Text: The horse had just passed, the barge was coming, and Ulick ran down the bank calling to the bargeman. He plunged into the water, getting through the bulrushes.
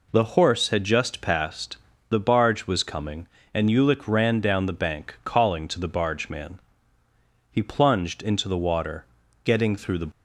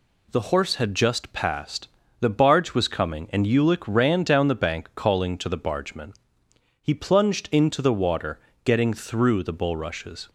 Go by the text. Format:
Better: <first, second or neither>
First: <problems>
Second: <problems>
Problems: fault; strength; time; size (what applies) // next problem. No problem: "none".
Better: second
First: stops before "bulrushes"; at 10.1 s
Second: none